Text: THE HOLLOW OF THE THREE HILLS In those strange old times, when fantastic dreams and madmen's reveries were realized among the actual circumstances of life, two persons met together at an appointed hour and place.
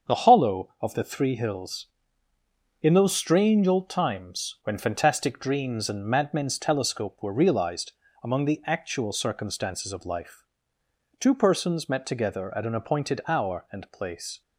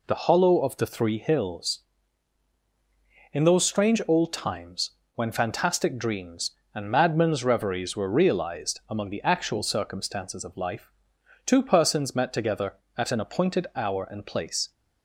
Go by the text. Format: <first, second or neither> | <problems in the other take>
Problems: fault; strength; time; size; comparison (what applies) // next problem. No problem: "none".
second | starts louder than the rest; until 1.2 s; 7 dB // says "telescope" for "reveries"; at 6.5 s // pauses between "realized" and "among"; slight; at 7.9 s; 0.30 s long